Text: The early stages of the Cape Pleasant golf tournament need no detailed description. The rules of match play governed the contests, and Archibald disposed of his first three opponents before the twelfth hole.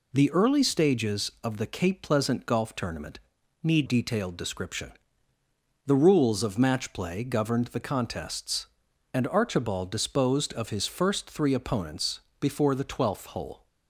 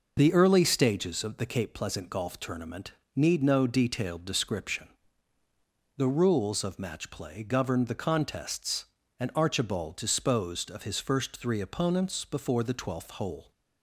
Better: second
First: pauses between "tournament" and "need"; at 3.1 s; 0.42 s long // skips "no"; at 3.8 s // pauses between "opponents" and "before"; slight; at 12.2 s; 0.20 s long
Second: pauses between "tournament" and "need"; slight; at 2.9 s; 0.24 s long

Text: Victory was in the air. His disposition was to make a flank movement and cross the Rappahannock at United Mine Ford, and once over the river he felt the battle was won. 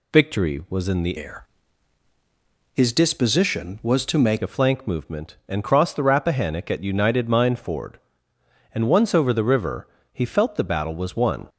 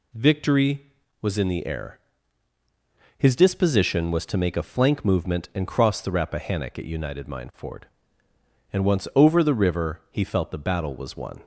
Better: second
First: changes voice from "air" to "make"; from 1.1 to 4.4 s; 3.3 s long // pauses between "river" and "he"; slight; at 9.8 s; 0.26 s long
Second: none

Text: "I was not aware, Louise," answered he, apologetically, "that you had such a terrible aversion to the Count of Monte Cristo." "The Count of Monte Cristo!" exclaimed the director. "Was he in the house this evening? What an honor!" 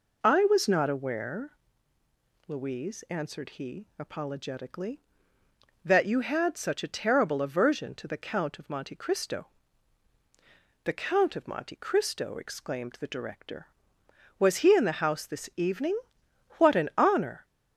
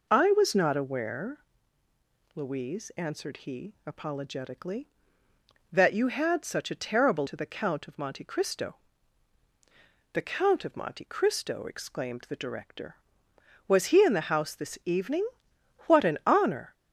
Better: first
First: none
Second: skips "aversion"; at 7.2 s

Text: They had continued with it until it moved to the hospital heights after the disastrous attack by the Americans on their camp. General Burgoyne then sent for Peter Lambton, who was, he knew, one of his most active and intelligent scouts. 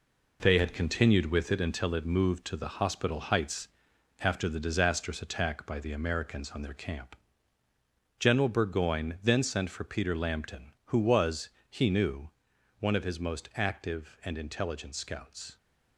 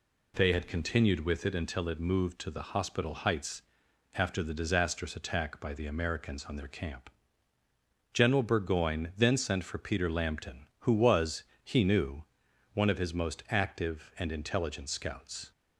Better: second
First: gets quieter; strong; throughout; 7 dB // pauses between "heights" and "after"; noticeable; at 3.6 s; 0.54 s long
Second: pauses between "heights" and "after"; noticeable; at 3.6 s; 0.54 s long

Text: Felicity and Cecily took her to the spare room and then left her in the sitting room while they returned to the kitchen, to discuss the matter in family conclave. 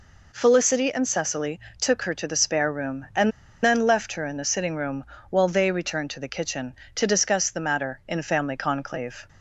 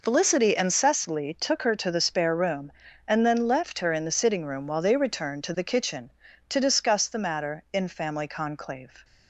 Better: second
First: pauses between "Cecily" and "took"; slight; at 1.6 s; 0.18 s long // pauses between "and" and "then"; slight; at 3.3 s; 0.34 s long // pauses between "room" and "while"; slight; at 5.0 s; 0.24 s long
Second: none

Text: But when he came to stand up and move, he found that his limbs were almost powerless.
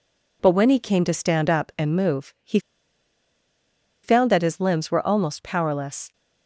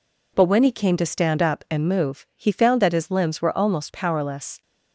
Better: second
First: pauses between "he" and "found"; strong; at 2.5 s; 1.4 s long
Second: none

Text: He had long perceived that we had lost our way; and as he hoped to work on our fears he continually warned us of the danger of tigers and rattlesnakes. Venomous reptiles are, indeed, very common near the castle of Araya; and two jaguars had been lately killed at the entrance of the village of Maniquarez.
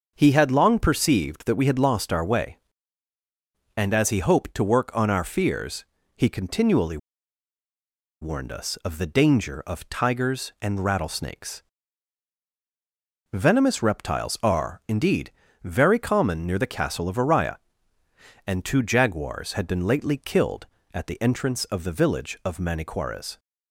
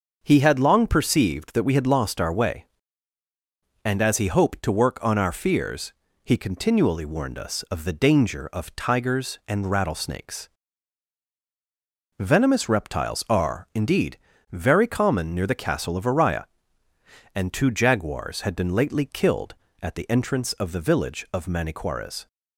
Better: second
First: starts louder than the rest; until 1.1 s; 6.5 dB // pauses between "fears" and "he"; slight; at 5.8 s; 0.30 s long // pauses between "continually" and "warned"; at 6.9 s; 1.2 s long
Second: starts louder than the rest; until 1.2 s; 6.5 dB // pauses between "fears" and "he"; slight; at 5.9 s; 0.30 s long

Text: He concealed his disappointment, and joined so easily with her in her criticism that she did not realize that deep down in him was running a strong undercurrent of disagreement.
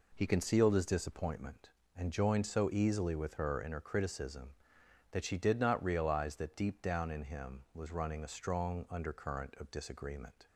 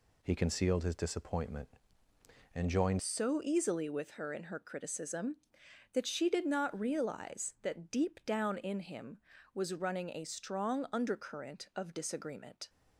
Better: first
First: none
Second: changes voice at "so"; from 2.9 s on; 9.7 s long

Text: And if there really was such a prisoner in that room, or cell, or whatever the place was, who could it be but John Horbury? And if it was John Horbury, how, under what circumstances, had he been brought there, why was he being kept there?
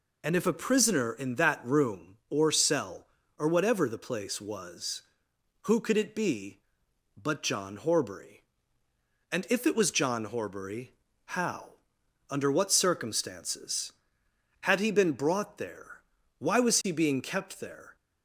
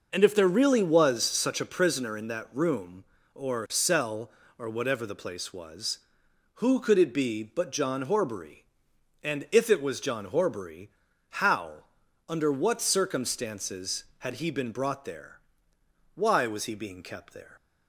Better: second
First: skips "there really was such"; at 0.4 s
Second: none

